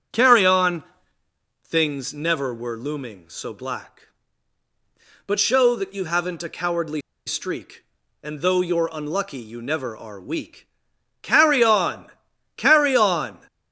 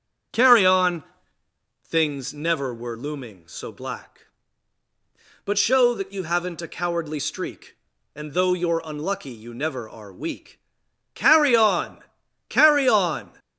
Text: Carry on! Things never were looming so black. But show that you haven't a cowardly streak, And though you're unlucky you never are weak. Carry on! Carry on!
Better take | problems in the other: second | starts louder than the rest; strong; until 1.9 s; 7.5 dB; strong in the second // pauses between "cowardly" and "streak"; slight; at 7.0 s; 0.25 s long

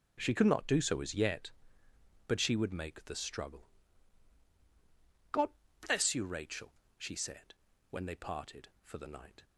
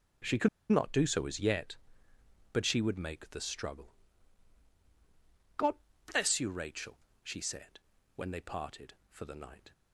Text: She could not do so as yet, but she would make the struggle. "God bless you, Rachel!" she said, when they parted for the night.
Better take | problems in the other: first | pauses between "could" and "not"; slight; at 0.4 s; 0.23 s long // pauses between "God" and "bless"; at 5.7 s; 0.38 s long; also in the first

